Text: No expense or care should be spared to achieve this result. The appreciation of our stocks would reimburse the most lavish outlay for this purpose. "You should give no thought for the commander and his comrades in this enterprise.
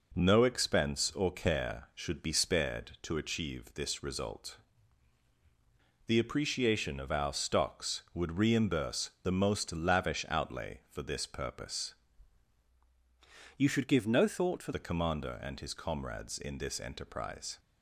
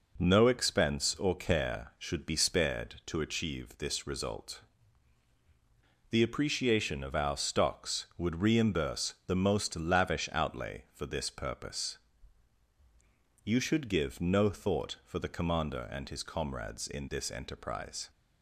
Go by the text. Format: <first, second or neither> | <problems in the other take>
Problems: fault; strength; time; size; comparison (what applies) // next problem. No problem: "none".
second | changes voice from "You" to "for"; from 13.5 to 14.7 s; 1.2 s long